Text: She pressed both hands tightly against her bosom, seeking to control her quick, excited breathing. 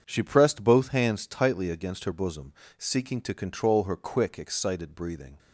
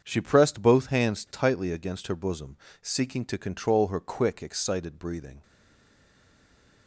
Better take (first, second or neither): first